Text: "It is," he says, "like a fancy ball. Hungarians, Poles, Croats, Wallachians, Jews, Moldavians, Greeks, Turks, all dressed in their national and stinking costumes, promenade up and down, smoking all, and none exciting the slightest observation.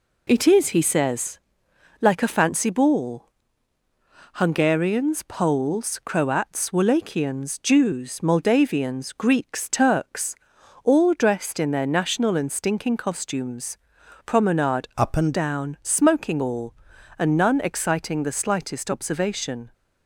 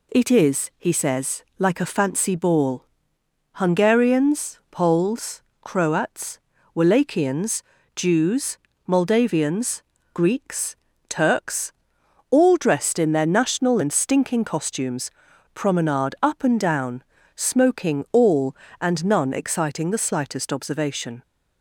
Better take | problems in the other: second | changes voice from "up" to "and"; from 14.9 to 15.3 s; 0.4 s long

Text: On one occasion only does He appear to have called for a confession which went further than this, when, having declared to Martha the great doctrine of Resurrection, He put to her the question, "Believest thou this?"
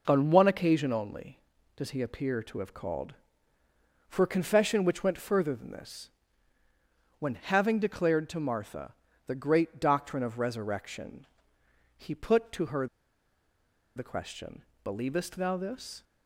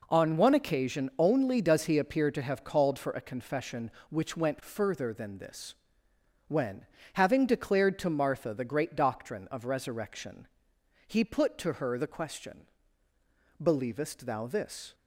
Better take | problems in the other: second | pauses between "Martha" and "the"; slight; at 8.9 s; 0.34 s long // pauses between "her" and "the"; at 12.8 s; 1.1 s long

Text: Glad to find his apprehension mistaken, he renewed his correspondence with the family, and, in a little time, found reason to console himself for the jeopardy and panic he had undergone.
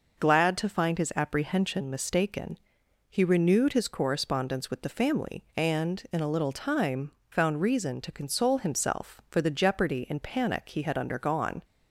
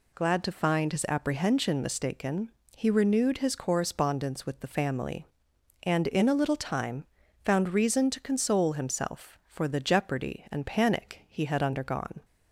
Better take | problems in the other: neither | none

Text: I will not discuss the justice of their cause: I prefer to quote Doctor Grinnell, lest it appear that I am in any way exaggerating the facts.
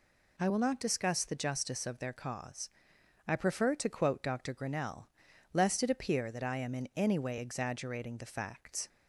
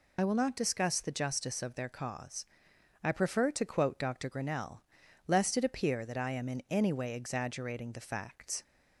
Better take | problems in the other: first | loses the start of "I"; at 0.1 s; 45 ms

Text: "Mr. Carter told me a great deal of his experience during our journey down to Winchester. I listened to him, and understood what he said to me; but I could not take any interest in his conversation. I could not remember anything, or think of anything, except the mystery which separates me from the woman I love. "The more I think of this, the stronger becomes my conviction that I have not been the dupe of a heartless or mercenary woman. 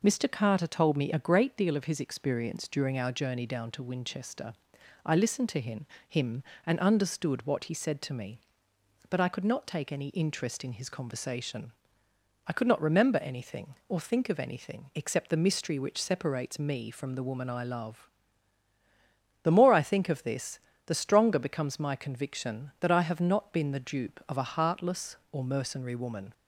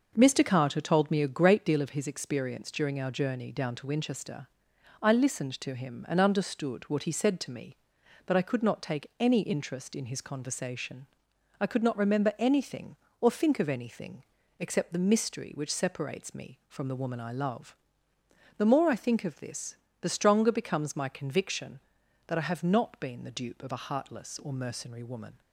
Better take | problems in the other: second | says "him" twice; at 6.0 s

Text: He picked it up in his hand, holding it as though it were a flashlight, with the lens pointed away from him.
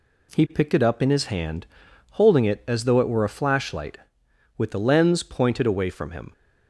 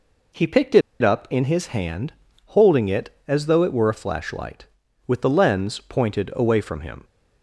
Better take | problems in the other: first | pauses between "it" and "up"; slight; at 0.8 s; 0.21 s long

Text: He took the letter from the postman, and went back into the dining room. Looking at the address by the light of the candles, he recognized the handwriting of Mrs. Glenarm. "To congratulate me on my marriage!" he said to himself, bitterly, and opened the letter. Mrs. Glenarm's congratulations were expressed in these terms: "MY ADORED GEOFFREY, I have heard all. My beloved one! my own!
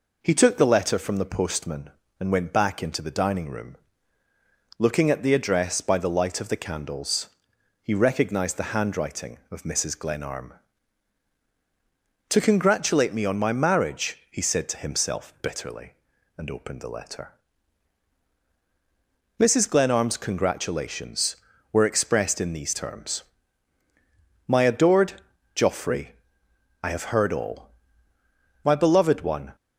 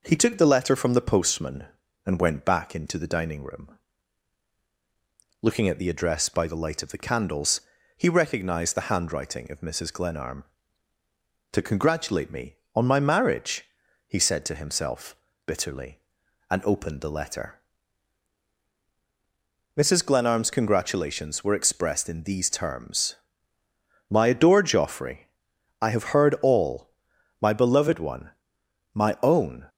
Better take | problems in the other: second | pauses between "ADORED" and "GEOFFREY"; at 25.1 s; 0.42 s long // stops before "my own"; at 29.5 s

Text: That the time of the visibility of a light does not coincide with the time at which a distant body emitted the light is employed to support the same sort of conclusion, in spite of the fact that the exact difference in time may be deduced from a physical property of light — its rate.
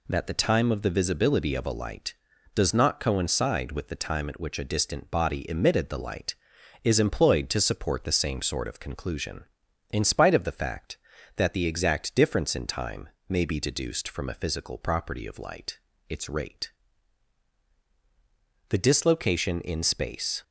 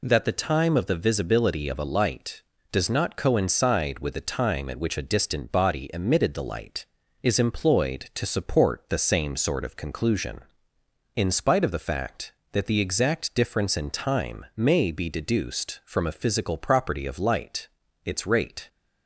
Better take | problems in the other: second | pauses between "time" and "may"; slight; at 13.0 s; 0.20 s long // goes on to say "The dislocation in space"; strong; from 18.6 s on; 1.7 s long

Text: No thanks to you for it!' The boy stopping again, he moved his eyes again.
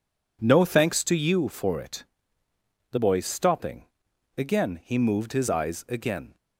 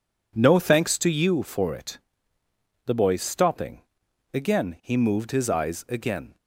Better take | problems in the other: neither | pauses between "stopping" and "again"; noticeable; the same in both

